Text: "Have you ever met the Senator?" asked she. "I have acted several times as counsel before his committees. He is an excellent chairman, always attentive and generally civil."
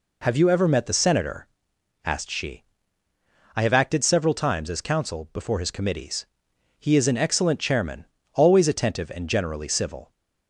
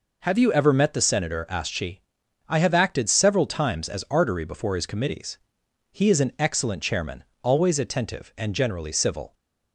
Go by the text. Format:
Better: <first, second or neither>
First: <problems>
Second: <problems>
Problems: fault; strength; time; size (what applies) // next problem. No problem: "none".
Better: first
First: none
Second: says "artery" for "counsel"; at 4.0 s